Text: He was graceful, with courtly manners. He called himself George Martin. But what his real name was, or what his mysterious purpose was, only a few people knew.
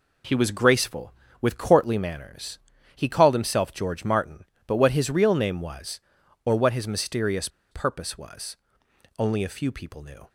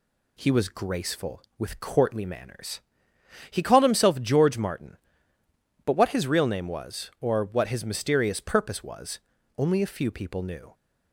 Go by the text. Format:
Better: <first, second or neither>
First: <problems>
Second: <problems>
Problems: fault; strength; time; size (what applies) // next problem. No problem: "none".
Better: second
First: pauses between "mysterious" and "purpose"; slight; at 7.4 s; 0.23 s long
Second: none